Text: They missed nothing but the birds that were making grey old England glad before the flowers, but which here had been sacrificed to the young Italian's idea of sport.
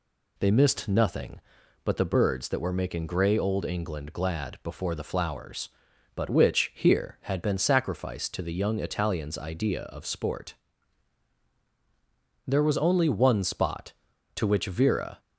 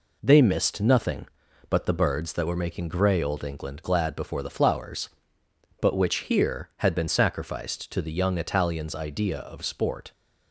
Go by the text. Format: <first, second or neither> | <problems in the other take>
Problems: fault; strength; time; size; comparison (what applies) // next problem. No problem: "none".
second | goes on to say "There was only one spot to which Vera"; strong; from 12.4 s on; 2.7 s long